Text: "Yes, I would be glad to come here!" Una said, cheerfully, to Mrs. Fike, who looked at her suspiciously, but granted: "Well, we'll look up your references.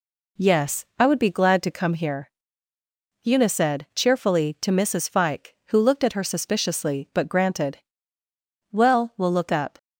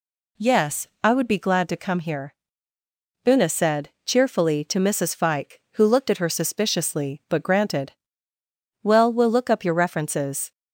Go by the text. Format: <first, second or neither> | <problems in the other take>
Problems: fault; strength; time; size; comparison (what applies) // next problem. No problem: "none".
second | stops before "your references"; at 9.7 s